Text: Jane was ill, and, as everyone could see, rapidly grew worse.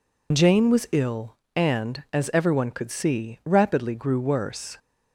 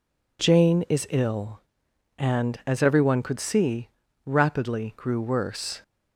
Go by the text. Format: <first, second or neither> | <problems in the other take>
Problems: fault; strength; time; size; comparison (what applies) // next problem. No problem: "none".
first | says "is" for "was"; at 0.8 s